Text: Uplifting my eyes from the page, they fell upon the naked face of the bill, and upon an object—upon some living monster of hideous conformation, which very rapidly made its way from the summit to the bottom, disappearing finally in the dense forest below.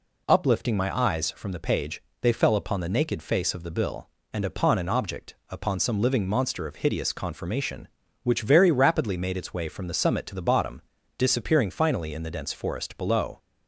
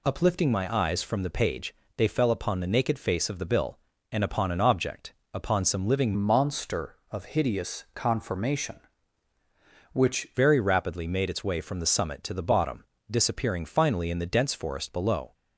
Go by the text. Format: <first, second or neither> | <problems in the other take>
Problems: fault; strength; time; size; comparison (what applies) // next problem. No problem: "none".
first | changes voice from "monster" to "which"; from 6.1 to 10.2 s; 4.1 s long